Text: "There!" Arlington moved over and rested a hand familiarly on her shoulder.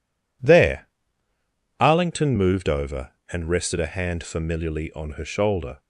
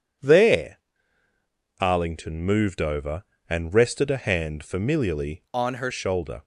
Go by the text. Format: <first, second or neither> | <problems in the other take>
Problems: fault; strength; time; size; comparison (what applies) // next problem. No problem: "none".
first | changes voice from "on" to "her"; from 5.5 to 5.9 s; 0.4 s long